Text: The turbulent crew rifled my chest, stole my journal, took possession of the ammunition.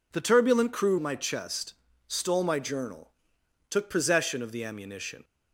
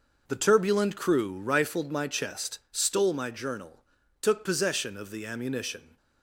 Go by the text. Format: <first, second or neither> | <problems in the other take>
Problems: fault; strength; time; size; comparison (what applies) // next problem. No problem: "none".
second | skips "rifled"; at 0.9 s